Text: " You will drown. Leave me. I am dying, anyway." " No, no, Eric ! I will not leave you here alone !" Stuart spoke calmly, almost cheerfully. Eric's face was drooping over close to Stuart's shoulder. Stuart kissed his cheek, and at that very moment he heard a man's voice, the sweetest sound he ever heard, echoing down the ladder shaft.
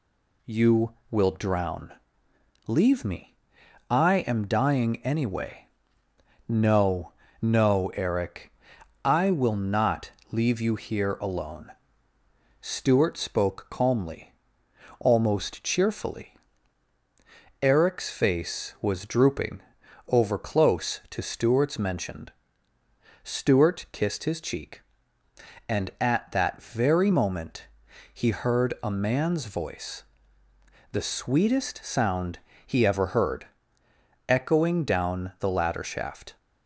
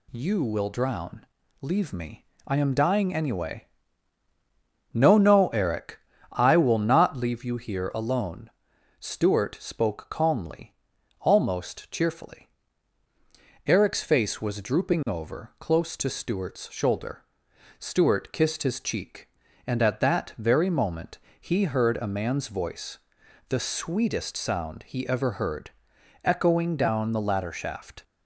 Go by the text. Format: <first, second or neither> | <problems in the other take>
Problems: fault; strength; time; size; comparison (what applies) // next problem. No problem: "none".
second | pauses between "not" and "leave"; slight; at 10.1 s; 0.20 s long // pauses between "drooping" and "over"; noticeable; at 19.6 s; 0.46 s long // says "mentioned" for "shoulder"; at 21.7 s // pauses between "moment" and "he"; noticeable; at 27.6 s; 0.46 s long; slight in the second // pauses between "sound" and "he"; slight; at 32.3 s; 0.26 s long